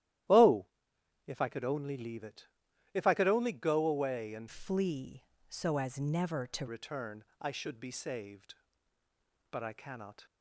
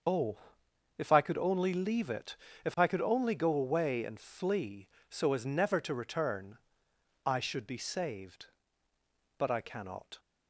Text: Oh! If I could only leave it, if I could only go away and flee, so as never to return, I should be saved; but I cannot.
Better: second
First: starts louder than the rest; strong; until 1.9 s; 13 dB // changes voice from "flee" to "to"; from 4.4 to 6.6 s; 2.2 s long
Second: starts louder than the rest; until 1.6 s; 6.5 dB

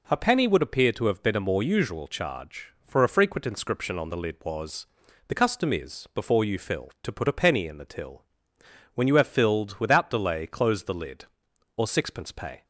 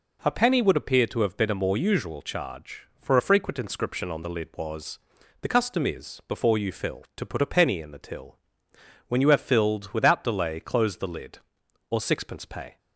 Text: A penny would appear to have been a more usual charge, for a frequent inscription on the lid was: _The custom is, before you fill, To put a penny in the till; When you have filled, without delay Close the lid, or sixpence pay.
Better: neither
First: none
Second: none

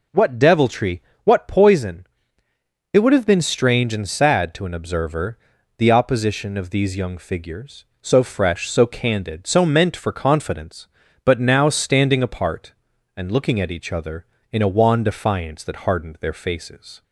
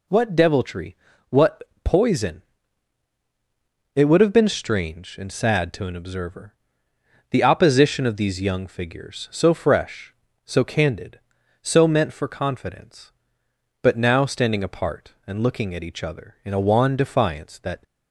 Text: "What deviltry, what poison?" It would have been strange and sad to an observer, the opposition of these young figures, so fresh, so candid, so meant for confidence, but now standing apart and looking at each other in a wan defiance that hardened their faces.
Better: first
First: none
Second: pauses between "what" and "poison"; slight; at 1.6 s; 0.20 s long // stops before "hardened their faces"; at 17.8 s

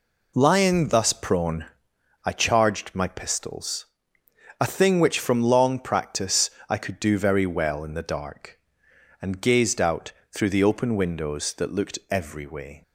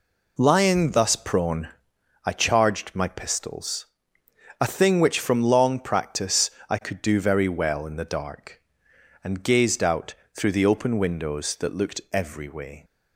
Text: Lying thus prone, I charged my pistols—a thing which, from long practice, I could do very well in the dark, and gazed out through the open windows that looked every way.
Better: neither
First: pauses between "out" and "through"; slight; at 10.1 s; 0.20 s long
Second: pauses between "out" and "through"; slight; at 10.1 s; 0.20 s long

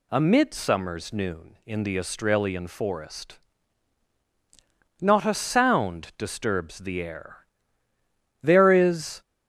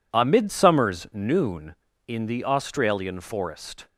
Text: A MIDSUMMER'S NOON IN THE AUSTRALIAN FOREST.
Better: second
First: goes on to say "Not a sound disturbs the air There is"; strong; from 5.0 s on; 4.2 s long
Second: none

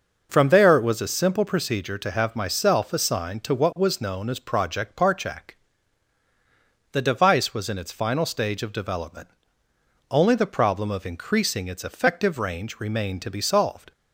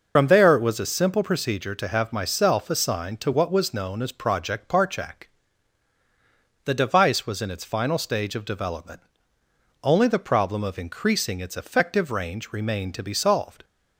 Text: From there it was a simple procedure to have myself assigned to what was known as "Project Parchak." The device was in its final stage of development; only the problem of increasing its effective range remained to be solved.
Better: first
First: none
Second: loses the start of "From"; at 0.1 s; 65 ms

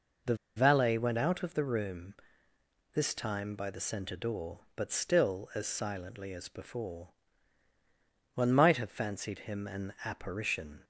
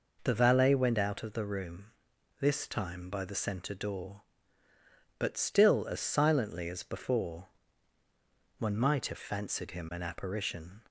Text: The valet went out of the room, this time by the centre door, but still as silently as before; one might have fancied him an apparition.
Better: second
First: pauses between "The" and "valet"; slight; at 0.3 s; 0.21 s long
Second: none

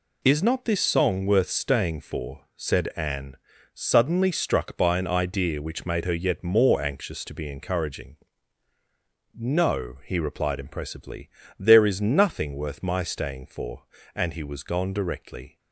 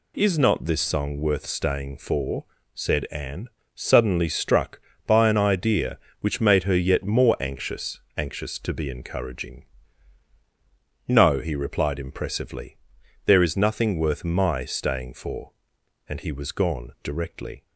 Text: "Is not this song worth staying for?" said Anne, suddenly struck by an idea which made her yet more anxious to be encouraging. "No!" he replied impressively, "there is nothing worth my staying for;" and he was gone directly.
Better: first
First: none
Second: says "anxious" twice; at 8.1 s

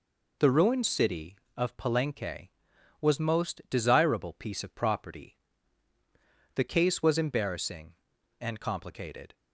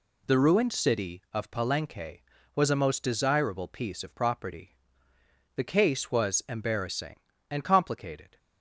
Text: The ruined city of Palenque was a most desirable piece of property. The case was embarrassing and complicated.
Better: second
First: skips "a"; at 3.2 s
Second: none

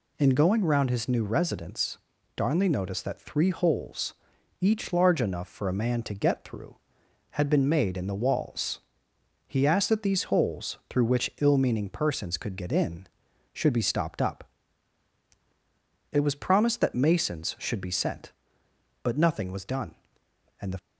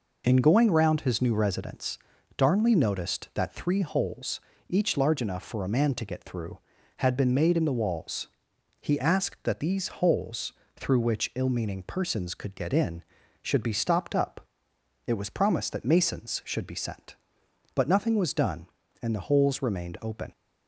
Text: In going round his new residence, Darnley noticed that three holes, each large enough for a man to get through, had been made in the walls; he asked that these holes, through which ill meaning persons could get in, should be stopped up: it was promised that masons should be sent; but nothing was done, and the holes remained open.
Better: second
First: stops before "holes remained open"; at 20.7 s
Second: none

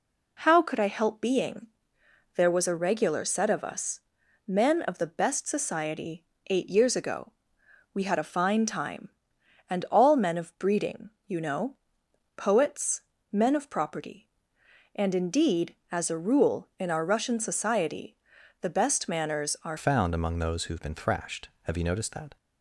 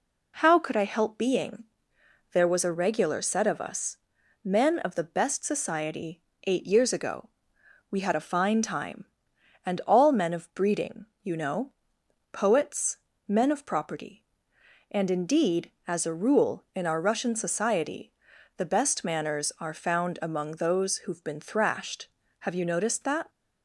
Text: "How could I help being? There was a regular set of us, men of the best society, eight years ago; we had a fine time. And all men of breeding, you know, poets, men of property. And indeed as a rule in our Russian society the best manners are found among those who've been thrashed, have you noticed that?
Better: second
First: pauses between "society" and "the"; at 18.1 s; 0.44 s long // changes voice at "found"; from 19.7 s on; 2.6 s long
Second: pauses between "society" and "the"; at 18.1 s; 0.44 s long

